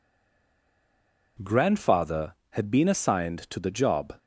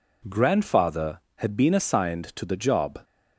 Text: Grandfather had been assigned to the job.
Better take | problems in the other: second | stays silent before the first word; noticeable; until 1.3 s; 1.3 s long

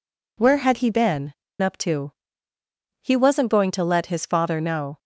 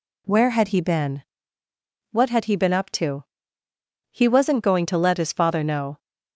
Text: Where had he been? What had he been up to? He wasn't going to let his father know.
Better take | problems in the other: second | skips "What had he been"; at 1.4 s

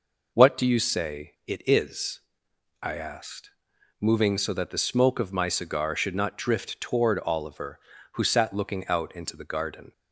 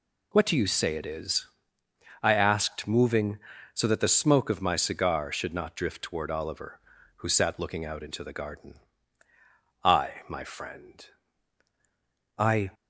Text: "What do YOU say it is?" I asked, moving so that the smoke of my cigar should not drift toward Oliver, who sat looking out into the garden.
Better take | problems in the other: first | goes on to say "I my friend I"; strong; from 9.8 s on; 2.8 s long

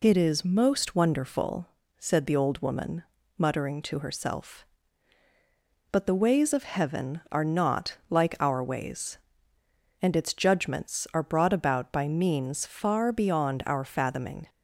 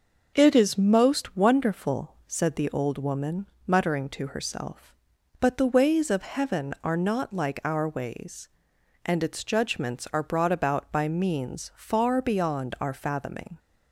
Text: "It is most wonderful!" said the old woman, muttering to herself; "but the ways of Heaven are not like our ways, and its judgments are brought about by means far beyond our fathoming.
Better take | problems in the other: neither | none

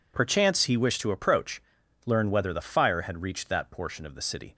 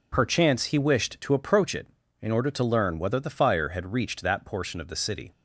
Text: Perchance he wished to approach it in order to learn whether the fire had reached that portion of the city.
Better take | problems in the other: second | skips "it in order to"; at 1.8 s

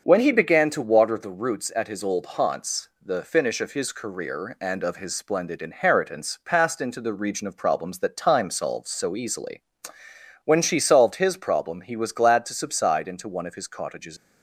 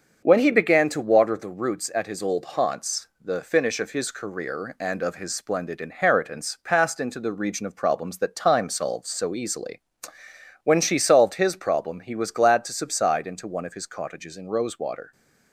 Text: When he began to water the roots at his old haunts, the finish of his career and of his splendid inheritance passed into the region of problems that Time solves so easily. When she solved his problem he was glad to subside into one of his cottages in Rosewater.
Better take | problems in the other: second | starts louder than the rest; until 1.0 s; 6.5 dB; also in the second // stops before "in Rosewater"; at 14.1 s

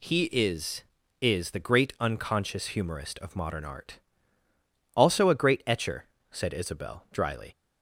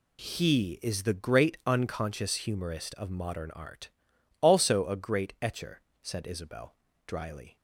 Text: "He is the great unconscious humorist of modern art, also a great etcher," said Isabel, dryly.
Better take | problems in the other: second | says "is" twice; at 1.2 s

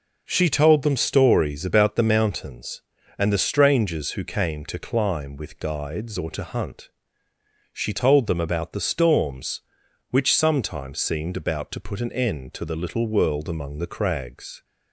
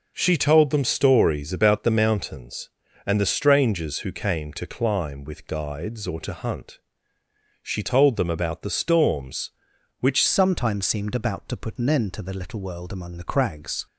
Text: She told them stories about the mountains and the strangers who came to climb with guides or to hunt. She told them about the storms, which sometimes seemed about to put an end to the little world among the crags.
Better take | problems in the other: first | changes voice at "sometimes"; from 10.2 s on; 3.6 s long

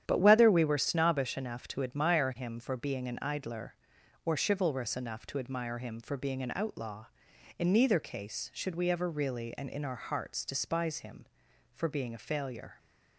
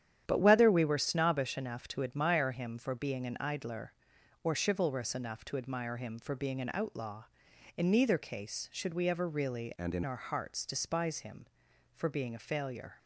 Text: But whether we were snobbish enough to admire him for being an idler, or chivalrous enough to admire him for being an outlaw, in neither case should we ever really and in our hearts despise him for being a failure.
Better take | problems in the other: first | starts louder than the rest; strong; until 1.2 s; 9.5 dB; strong in the first // changes voice from "and" to "in"; from 9.7 to 10.0 s; 0.3 s long

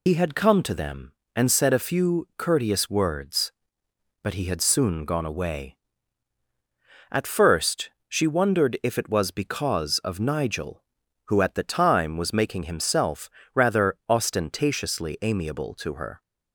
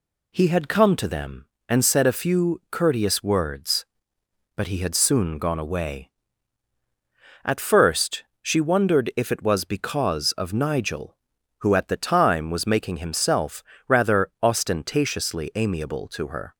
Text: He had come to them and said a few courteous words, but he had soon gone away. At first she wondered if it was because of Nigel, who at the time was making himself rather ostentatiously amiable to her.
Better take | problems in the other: second | loses the start of "He"; at 0.0 s; 50 ms // pauses between "first" and "she"; slight; at 7.8 s; 0.18 s long; slight in the second // pauses between "himself" and "rather"; slight; at 13.2 s; 0.24 s long; slight in the second

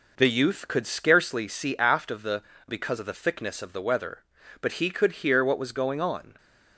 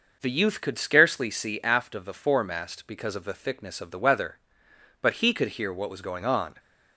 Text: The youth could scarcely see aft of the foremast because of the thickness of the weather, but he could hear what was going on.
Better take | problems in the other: second | skips "foremast"; at 2.5 s

